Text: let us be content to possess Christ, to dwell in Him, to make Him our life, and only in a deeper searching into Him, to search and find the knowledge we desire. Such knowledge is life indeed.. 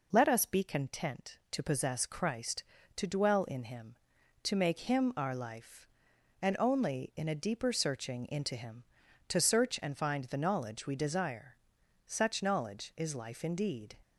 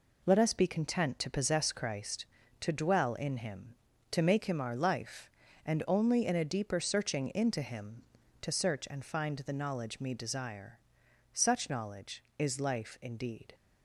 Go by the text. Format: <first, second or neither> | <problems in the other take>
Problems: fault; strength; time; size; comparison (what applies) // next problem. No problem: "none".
first | says "me" for "we"; at 9.9 s